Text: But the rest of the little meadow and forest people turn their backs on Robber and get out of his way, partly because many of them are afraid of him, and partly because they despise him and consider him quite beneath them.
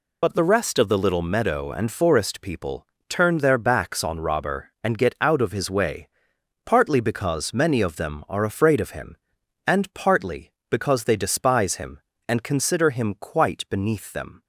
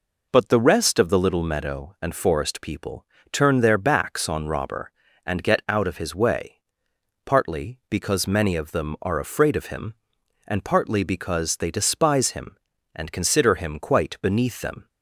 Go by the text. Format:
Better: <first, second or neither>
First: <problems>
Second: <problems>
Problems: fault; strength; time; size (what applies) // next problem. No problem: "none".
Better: second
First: loses the start of "But"; at 0.2 s; 75 ms // pauses between "people" and "turn"; slight; at 2.8 s; 0.22 s long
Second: pauses between "people" and "turn"; slight; at 3.0 s; 0.26 s long